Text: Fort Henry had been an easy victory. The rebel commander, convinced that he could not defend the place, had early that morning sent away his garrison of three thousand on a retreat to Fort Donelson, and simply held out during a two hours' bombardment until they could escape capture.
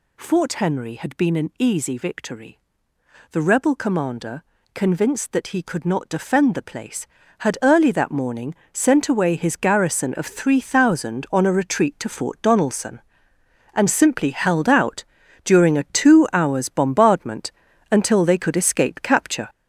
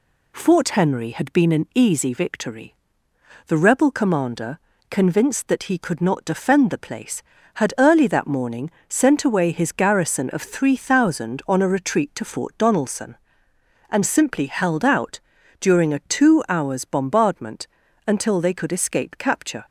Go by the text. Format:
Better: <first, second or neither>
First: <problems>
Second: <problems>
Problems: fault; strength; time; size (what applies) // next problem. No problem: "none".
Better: second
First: gets louder; throughout; 6 dB // pauses between "morning" and "sent"; slight; at 8.5 s; 0.20 s long // pauses between "out" and "during"; at 15.0 s; 0.40 s long // pauses between "bombardment" and "until"; at 17.5 s; 0.40 s long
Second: pauses between "morning" and "sent"; slight; at 8.6 s; 0.20 s long // pauses between "out" and "during"; at 15.1 s; 0.40 s long // pauses between "bombardment" and "until"; at 17.6 s; 0.40 s long